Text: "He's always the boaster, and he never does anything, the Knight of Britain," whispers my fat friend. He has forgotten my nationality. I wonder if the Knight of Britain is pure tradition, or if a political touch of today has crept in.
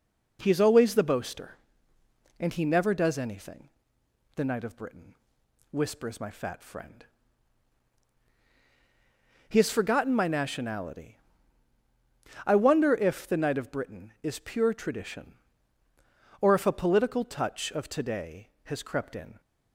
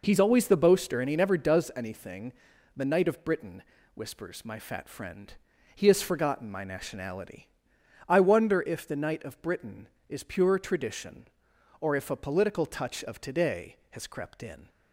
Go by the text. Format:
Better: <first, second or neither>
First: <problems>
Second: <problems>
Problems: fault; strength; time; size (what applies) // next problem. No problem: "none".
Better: neither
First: none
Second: none